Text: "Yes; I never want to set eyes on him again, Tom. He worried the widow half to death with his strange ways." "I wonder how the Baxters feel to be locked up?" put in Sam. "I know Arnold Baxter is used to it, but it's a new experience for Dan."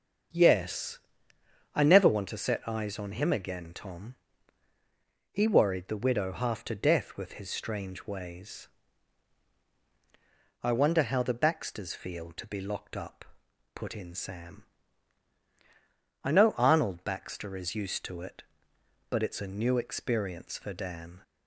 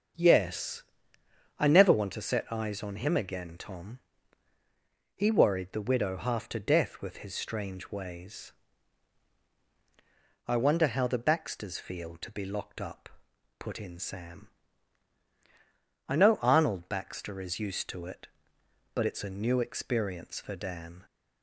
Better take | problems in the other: neither | starts louder than the rest; the same in both

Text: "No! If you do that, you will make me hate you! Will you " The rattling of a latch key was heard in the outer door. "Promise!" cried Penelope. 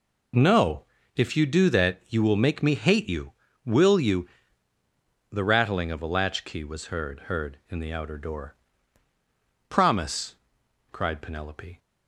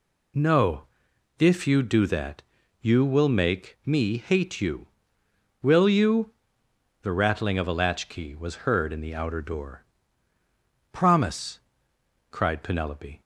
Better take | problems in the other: second | says "heard" twice; at 7.3 s

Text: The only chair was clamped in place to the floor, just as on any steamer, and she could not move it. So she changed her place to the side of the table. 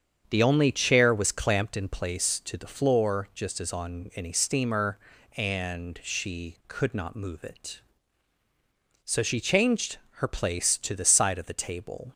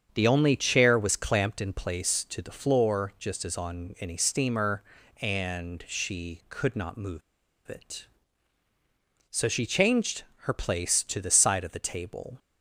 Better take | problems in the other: first | starts louder than the rest; strong; until 1.1 s; 7.5 dB; strong in the first // pauses between "move" and "it"; noticeable; at 7.2 s; 0.47 s long // pauses between "changed" and "her"; slight; at 10.2 s; 0.20 s long; slight in the first

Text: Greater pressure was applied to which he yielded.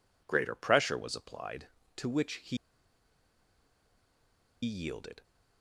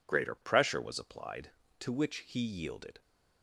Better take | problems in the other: second | pauses between "he" and "yielded"; strong; at 2.5 s; 2.0 s long

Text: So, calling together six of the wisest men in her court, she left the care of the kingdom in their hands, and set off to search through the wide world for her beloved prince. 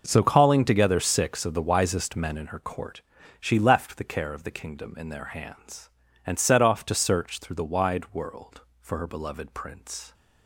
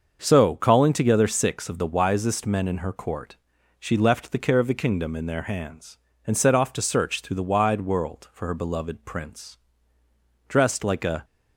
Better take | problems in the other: first | starts louder than the rest; until 1.2 s; 6.5 dB // goes on to say "Dressed like a"; noticeable; from 10.4 s on; 0.78 s long

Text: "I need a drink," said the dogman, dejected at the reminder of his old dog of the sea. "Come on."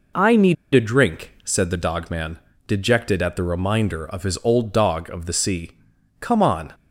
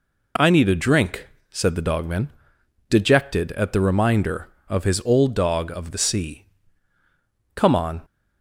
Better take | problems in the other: second | pauses between "need" and "a"; slight; at 0.5 s; 0.19 s long

